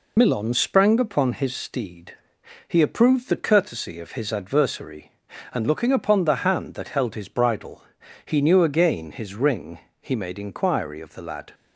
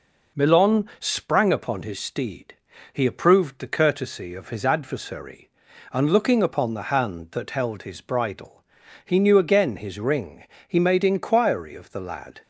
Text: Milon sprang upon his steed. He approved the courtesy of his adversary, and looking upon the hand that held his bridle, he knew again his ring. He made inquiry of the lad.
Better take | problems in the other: second | loses the start of "Milon"; at 0.1 s; 50 ms

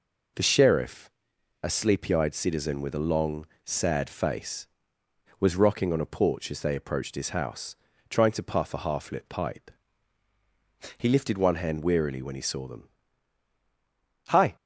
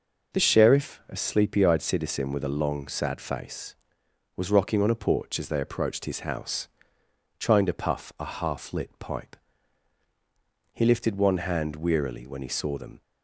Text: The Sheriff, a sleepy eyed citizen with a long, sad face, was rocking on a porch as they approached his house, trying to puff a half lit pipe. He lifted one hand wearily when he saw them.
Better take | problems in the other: second | goes on to say "Hi"; slight; from 14.2 s on; 0.26 s long

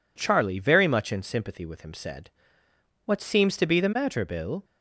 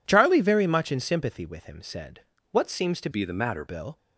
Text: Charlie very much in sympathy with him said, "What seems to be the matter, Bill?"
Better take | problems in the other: first | changes voice from "be" to "matter"; from 3.1 to 3.6 s; 0.5 s long

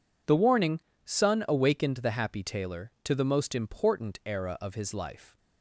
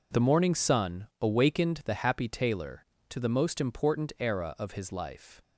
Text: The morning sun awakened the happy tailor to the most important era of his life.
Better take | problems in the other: second | says "warning" for "morning"; at 0.3 s

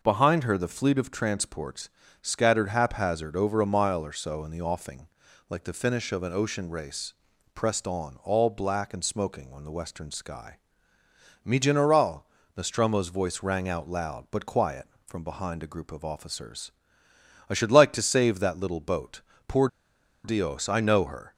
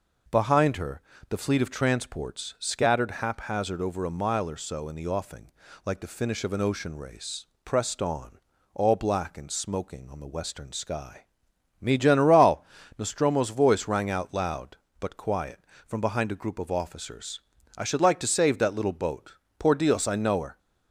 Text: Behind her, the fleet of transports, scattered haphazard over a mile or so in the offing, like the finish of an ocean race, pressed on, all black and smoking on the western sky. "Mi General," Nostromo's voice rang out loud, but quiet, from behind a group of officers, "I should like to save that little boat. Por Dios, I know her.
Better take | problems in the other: second | pauses between "Por" and "Dios"; noticeable; at 19.6 s; 0.56 s long

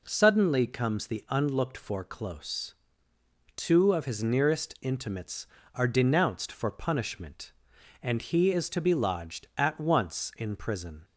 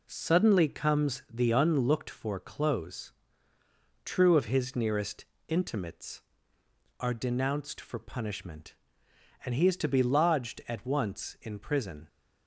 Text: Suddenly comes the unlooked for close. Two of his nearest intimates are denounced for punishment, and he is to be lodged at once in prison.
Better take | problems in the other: first | says "True" for "Two"; at 4.0 s // pauses between "nearest" and "intimates"; slight; at 5.2 s; 0.22 s long

